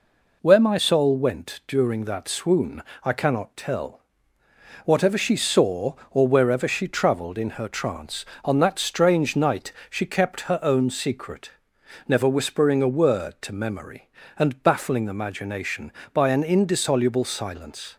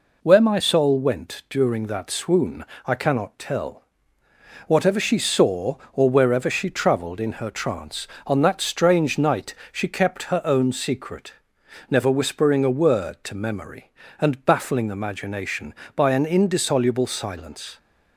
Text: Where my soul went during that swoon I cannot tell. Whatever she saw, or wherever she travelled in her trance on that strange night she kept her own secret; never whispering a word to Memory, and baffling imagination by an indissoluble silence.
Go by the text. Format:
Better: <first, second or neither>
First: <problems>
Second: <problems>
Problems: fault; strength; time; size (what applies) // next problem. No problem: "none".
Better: neither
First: pauses between "swoon" and "I"; slight; at 2.8 s; 0.22 s long // pauses between "night" and "she"; slight; at 9.7 s; 0.18 s long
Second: pauses between "swoon" and "I"; slight; at 2.6 s; 0.22 s long // pauses between "night" and "she"; slight; at 9.5 s; 0.18 s long